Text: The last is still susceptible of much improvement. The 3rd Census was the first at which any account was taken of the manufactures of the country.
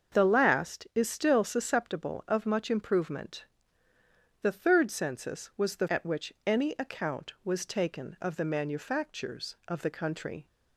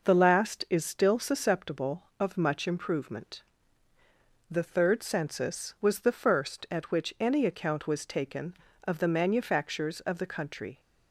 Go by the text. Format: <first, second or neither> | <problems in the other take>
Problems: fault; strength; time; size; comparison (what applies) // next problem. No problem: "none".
second | starts louder than the rest; until 1.1 s; 6.5 dB // skips "first"; at 5.8 s